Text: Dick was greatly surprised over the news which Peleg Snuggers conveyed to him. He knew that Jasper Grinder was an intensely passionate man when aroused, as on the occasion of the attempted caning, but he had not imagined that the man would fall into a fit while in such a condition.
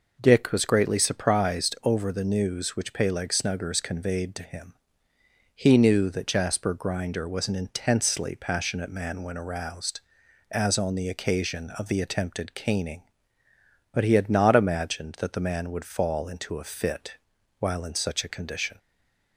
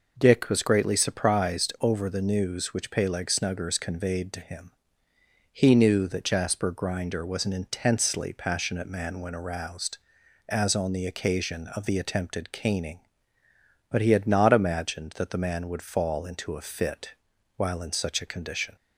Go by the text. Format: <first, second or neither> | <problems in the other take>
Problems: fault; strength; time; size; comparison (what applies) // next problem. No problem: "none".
second | pauses between "fit" and "while"; at 17.1 s; 0.44 s long; also in the second // stays silent after the last word; slight; from 18.7 s on; 0.6 s long